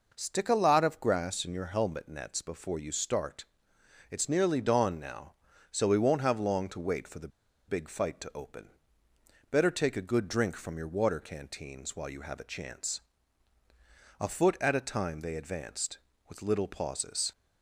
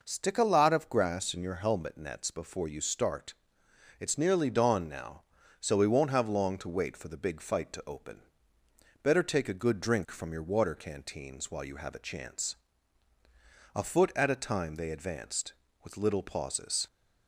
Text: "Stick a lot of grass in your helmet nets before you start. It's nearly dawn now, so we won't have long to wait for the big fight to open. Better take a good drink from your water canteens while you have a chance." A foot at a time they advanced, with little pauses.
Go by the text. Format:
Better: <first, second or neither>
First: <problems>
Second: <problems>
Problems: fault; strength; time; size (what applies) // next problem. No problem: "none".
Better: second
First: pauses between "the" and "big"; at 7.2 s; 0.39 s long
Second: none